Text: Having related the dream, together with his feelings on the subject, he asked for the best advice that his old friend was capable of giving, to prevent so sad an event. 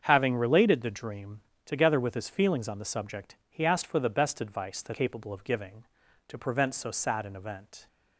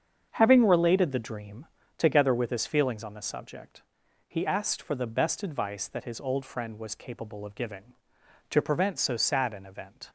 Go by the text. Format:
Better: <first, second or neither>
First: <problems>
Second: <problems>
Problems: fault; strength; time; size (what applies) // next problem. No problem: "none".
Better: second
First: starts louder than the rest; strong; until 1.0 s; 7.5 dB // skips "his old friend was"; at 4.9 s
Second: starts louder than the rest; strong; until 1.3 s; 7 dB